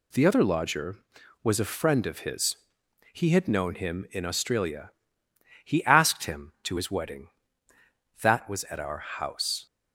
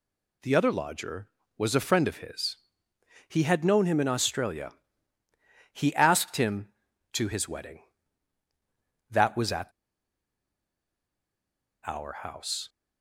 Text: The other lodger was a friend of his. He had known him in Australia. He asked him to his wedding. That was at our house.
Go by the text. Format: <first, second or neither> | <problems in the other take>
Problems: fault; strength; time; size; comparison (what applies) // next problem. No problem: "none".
first | pauses between "at" and "our"; strong; at 9.6 s; 2.1 s long